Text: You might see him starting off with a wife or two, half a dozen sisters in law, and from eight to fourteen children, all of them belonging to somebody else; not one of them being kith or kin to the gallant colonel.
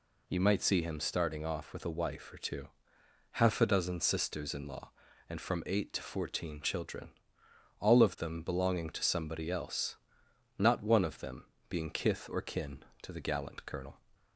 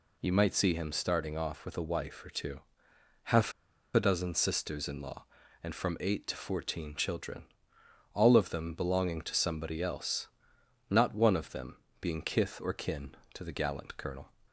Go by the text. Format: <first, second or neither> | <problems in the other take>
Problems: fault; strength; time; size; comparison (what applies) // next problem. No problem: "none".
first | pauses between "half" and "a"; at 3.5 s; 0.43 s long // pauses between "them" and "being"; slight; at 11.7 s; 0.24 s long; slight in the first